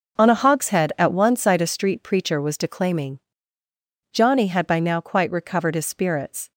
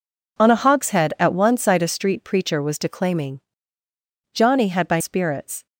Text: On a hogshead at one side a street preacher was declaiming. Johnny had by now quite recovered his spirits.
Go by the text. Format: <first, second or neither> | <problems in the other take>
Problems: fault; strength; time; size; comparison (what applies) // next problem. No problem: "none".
first | skips "now quite recovered his"; at 5.0 s